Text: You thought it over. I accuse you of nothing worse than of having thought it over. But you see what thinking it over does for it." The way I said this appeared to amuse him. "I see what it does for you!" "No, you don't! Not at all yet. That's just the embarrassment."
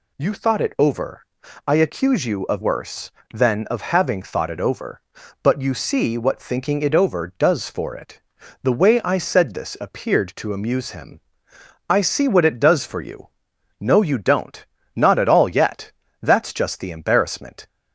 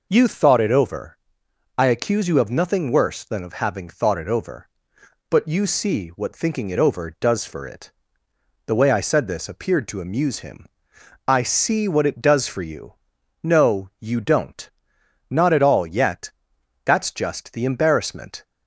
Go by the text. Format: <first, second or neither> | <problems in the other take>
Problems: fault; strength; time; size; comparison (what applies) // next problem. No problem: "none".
second | skips "nothing"; at 2.6 s